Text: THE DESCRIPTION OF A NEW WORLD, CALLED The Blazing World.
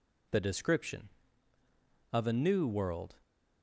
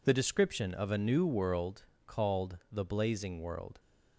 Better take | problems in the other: second | stops before "CALLED The Blazing World"; at 3.2 s

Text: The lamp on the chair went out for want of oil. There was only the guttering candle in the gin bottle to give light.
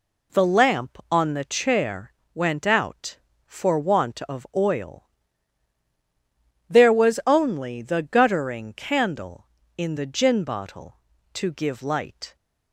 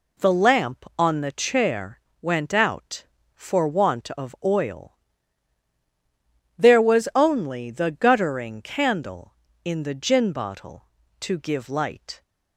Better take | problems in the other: neither | pauses between "chair" and "went"; slight; the same in both

